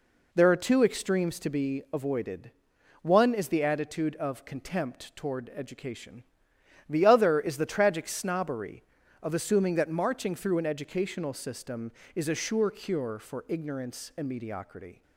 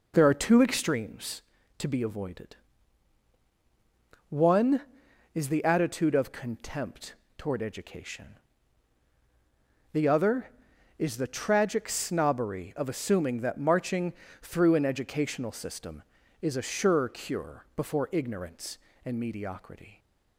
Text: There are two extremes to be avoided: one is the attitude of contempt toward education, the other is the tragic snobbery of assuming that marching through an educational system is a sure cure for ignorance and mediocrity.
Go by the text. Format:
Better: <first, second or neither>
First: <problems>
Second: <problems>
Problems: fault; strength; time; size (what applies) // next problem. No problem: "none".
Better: first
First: none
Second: pauses between "contempt" and "toward"; slight; at 7.1 s; 0.22 s long // pauses between "marching" and "through"; slight; at 14.1 s; 0.28 s long // says "before" for "for"; at 17.7 s